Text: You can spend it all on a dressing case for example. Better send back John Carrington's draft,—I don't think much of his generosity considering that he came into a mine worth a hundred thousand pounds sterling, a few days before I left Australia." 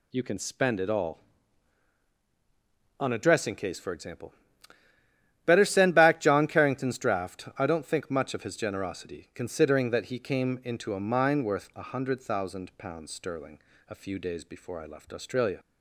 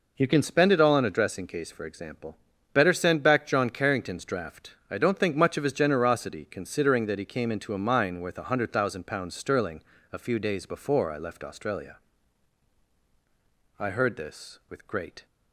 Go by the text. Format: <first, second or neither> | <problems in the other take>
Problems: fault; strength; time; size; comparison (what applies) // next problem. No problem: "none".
first | goes on to say "I heard this with great"; from 13.7 s on; 1.4 s long